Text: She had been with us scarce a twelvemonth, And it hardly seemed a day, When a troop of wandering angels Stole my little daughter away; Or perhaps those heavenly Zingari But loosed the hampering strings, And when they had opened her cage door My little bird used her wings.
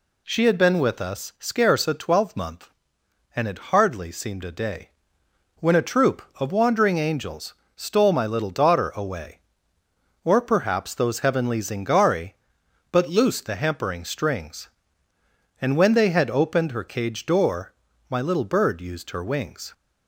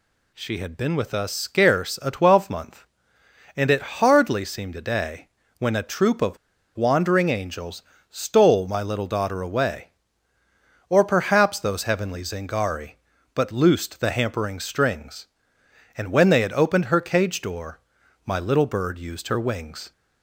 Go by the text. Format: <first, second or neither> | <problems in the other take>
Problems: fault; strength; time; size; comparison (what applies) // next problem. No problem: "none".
first | pauses between "of" and "wandering"; at 6.3 s; 0.39 s long // pauses between "angels" and "Stole"; slight; at 7.8 s; 0.28 s long; slight in the first // pauses between "door" and "My"; noticeable; at 17.7 s; 0.46 s long; slight in the first